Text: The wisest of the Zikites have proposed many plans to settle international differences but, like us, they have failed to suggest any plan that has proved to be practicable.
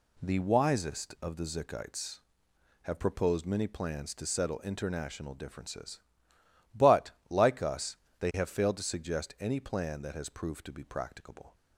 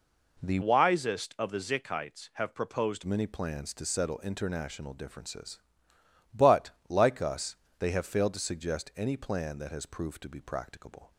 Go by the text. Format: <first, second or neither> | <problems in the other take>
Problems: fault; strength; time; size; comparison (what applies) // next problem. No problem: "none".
first | changes voice from "wisest" to "proposed"; from 0.6 to 3.0 s; 2.4 s long